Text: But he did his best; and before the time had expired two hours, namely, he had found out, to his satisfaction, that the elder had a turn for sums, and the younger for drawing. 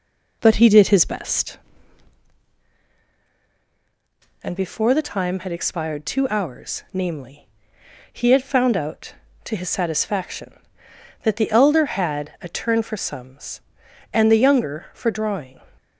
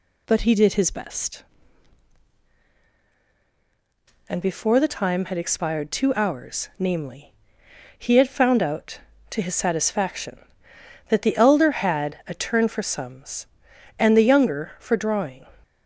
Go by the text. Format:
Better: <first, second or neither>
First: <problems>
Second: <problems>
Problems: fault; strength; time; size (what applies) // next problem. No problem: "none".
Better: second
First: starts louder than the rest; noticeable; until 2.3 s; 4 dB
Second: none